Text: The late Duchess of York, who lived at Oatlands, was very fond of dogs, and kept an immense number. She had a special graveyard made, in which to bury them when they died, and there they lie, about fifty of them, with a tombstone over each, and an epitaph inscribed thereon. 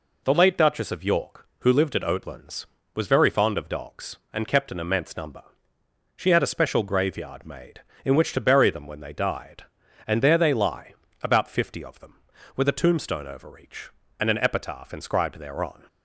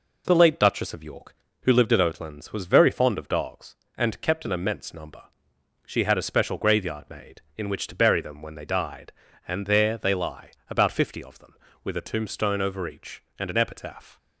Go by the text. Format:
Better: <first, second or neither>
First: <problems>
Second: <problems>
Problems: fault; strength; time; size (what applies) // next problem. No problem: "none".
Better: first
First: none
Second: stops before "inscribed thereon"; at 14.1 s